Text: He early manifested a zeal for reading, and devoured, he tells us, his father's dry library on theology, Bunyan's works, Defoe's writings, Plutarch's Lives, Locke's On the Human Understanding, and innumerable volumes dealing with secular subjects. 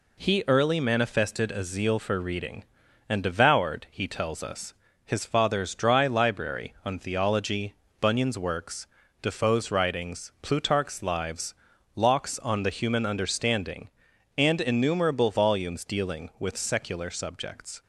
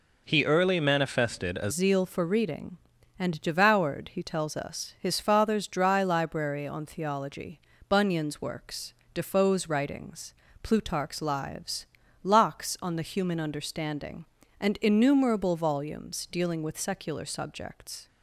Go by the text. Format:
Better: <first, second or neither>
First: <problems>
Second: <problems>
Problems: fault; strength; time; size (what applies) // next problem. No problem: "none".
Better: first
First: none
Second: changes voice at "zeal"; from 1.7 s on; 16.3 s long